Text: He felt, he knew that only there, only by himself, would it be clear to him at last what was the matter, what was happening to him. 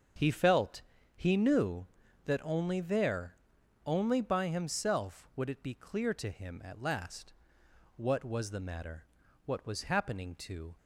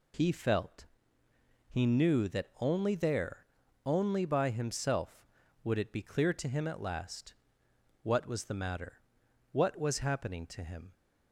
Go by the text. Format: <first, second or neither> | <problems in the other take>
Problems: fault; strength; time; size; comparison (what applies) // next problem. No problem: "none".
second | starts louder than the rest; until 1.5 s; 7 dB // pauses between "last" and "what"; noticeable; at 7.3 s; 0.64 s long; noticeable in the second // stops before "him"; at 10.7 s